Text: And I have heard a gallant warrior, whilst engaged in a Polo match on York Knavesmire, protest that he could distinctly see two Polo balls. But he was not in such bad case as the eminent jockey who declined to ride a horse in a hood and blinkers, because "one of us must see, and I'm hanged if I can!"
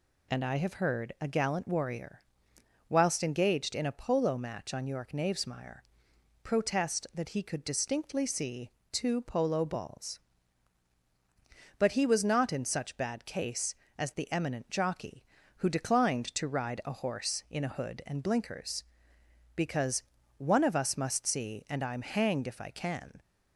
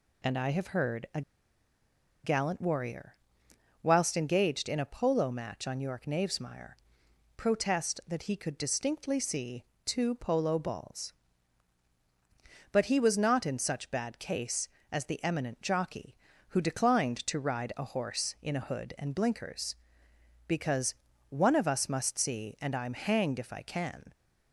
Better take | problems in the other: first | pauses between "a" and "gallant"; at 1.2 s; 1.0 s long // pauses between "see" and "two"; slight; at 9.6 s; 0.22 s long; slight in the first // pauses between "because" and "one"; slight; at 20.9 s; 0.36 s long; slight in the first

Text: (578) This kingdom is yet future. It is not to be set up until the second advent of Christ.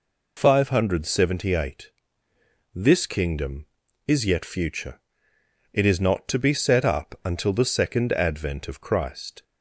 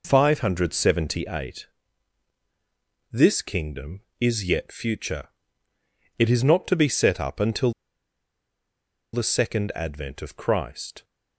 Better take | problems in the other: first | pauses between "until" and "the"; strong; at 7.7 s; 1.4 s long

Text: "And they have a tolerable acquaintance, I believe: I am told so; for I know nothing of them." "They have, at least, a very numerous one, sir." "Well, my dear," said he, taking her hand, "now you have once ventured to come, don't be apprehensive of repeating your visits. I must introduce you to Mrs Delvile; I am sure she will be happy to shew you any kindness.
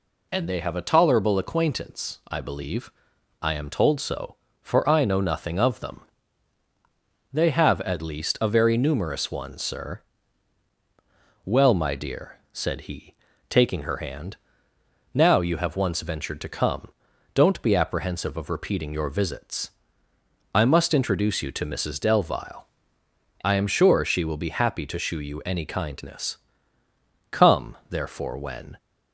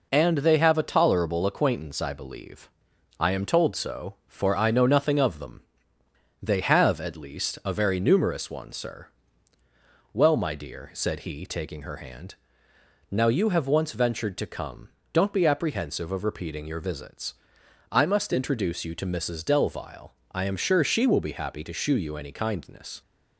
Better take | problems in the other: second | goes on to say "Come therefore when"; from 27.2 s on; 1.4 s long

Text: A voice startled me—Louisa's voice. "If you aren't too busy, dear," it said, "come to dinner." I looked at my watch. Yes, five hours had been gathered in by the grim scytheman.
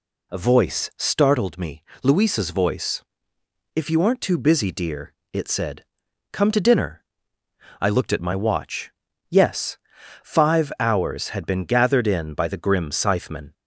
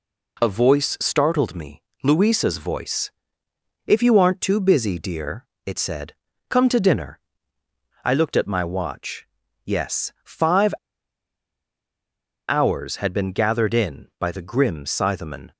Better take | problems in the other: first | pauses between "five" and "hours"; strong; at 10.7 s; 1.7 s long

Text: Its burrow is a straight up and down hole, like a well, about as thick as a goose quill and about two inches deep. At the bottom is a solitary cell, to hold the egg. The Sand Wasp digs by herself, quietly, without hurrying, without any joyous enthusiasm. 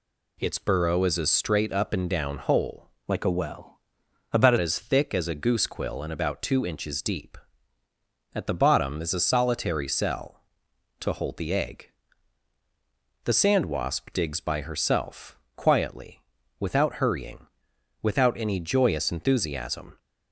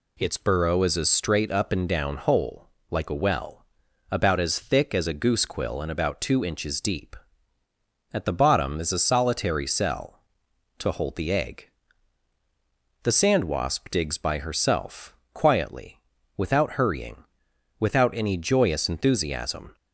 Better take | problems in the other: second | changes voice from "like" to "about"; from 3.0 to 4.5 s; 1.5 s long

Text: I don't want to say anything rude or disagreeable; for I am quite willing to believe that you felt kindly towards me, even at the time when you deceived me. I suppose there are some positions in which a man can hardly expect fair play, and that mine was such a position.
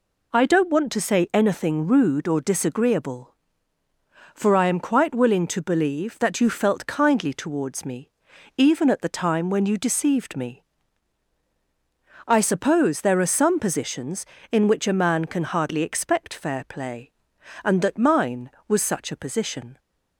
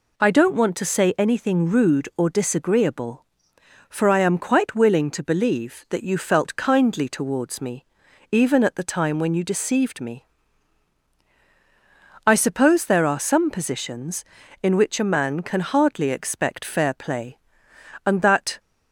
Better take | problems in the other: first | stops before "mine was such a position"; at 18.5 s

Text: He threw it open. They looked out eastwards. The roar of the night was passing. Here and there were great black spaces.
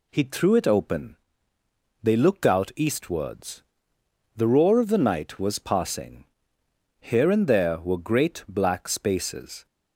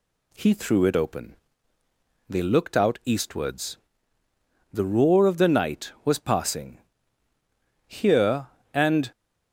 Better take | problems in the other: first | stops before "there were great black spaces"; at 9.1 s

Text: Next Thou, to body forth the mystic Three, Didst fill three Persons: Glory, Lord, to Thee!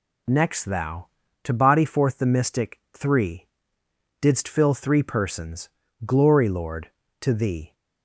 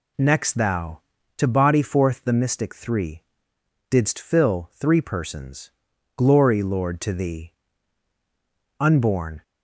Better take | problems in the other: first | goes on to say "Unborn"; noticeable; from 8.7 s on; 0.64 s long

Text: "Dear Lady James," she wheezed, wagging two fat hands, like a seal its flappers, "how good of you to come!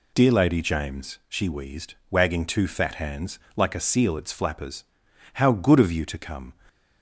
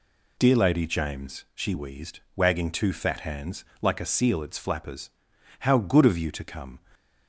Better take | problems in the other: neither | none

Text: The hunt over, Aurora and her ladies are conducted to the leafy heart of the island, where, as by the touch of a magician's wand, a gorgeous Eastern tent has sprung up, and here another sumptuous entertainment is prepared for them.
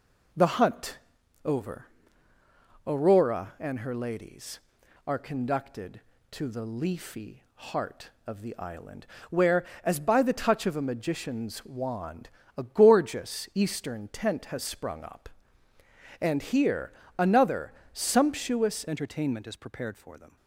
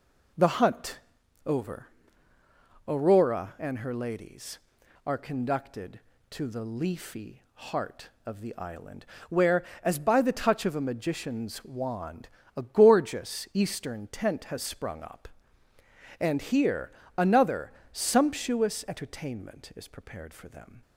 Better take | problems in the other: second | pauses between "hunt" and "over"; noticeable; at 0.9 s; 0.46 s long; noticeable in the second // pauses between "here" and "another"; slight; at 16.9 s; 0.24 s long; slight in the second // pauses between "another" and "sumptuous"; slight; at 17.7 s; 0.20 s long; slight in the second // changes voice at "entertainment"; from 18.8 s on; 1.5 s long

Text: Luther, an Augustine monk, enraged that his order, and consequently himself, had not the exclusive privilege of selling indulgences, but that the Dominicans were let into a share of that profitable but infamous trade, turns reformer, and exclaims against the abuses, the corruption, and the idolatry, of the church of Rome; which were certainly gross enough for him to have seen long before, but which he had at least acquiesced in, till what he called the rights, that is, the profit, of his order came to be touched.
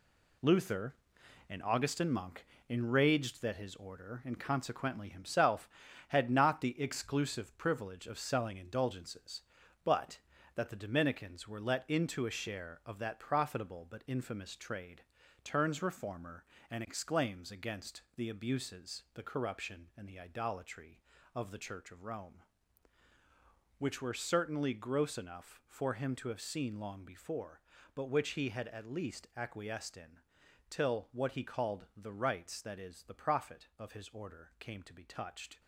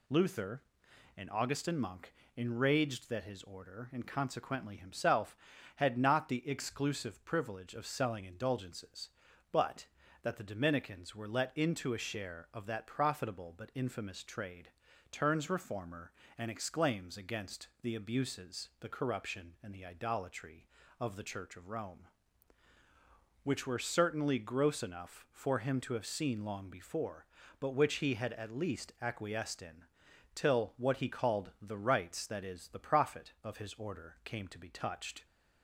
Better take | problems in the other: second | gets quieter; throughout; 7 dB

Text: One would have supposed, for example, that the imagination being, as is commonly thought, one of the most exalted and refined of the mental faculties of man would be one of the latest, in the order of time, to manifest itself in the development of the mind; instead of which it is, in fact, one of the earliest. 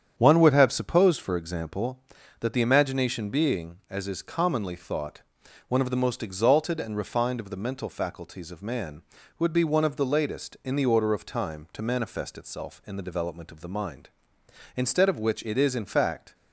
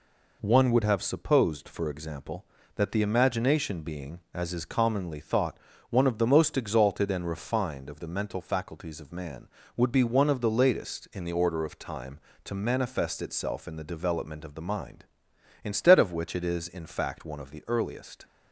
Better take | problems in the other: second | starts louder than the rest; strong; until 1.1 s; 8.5 dB // stops before "one of the earliest"; at 16.3 s

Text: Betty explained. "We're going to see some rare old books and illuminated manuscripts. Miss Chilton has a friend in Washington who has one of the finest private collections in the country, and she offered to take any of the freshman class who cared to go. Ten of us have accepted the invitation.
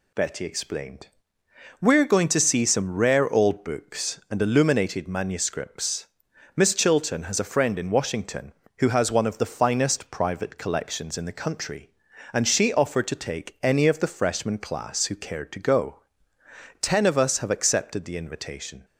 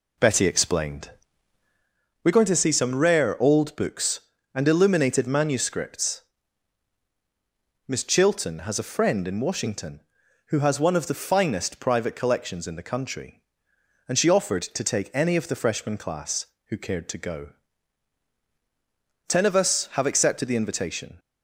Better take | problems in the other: first | starts louder than the rest; slight; until 2.0 s; 2.5 dB

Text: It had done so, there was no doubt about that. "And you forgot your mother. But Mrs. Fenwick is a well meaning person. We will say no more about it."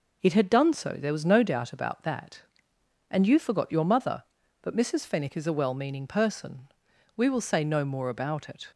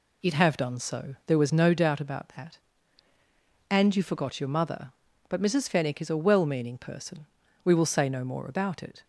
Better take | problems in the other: first | says "have" for "had"; at 0.3 s

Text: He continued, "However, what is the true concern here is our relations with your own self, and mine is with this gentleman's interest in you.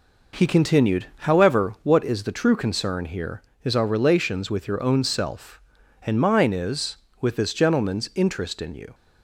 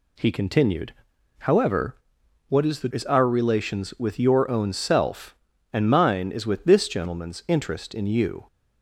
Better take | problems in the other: first | skips "true concern here"; at 2.9 s

